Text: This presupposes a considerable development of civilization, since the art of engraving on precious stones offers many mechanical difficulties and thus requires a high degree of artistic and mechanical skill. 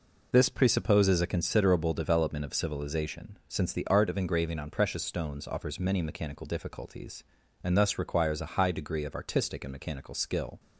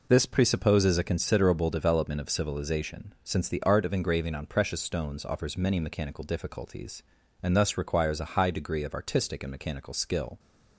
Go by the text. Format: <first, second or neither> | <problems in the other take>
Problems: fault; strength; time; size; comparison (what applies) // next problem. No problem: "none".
neither | none